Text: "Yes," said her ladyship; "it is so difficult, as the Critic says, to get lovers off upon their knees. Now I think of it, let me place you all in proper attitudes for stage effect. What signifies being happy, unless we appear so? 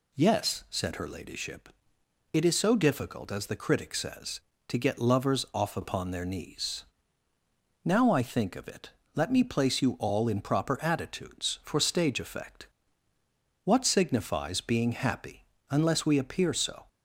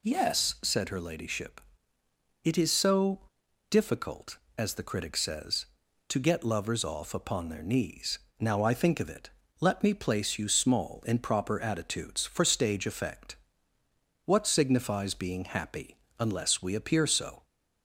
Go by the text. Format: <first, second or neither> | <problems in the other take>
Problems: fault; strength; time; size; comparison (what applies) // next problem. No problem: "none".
first | pauses between "so" and "difficult"; noticeable; at 3.2 s; 0.48 s long // says "small" for "all"; at 10.4 s